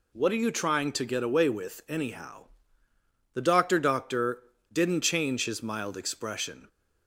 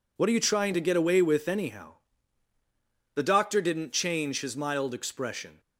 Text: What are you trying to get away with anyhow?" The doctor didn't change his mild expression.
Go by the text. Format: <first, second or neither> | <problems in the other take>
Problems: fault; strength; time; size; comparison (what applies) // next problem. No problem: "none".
second | says "doctor" twice; at 3.7 s